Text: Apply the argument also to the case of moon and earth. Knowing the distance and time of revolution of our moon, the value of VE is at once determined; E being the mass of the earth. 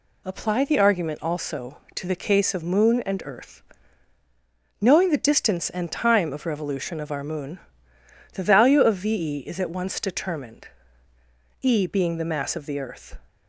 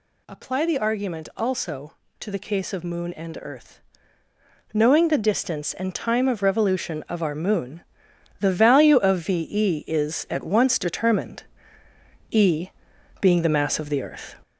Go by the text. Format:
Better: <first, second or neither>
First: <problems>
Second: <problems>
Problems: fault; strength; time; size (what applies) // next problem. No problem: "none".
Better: first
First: none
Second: gets louder; noticeable; throughout; 4.5 dB // pauses between "E" and "being"; noticeable; at 12.7 s; 0.50 s long